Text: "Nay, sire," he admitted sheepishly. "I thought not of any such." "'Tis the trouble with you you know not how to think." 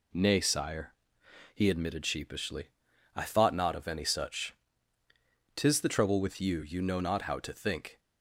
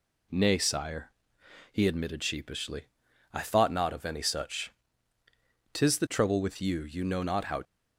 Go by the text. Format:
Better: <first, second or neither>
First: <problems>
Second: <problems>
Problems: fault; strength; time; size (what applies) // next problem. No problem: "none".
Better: first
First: none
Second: stops before "to think"; at 7.6 s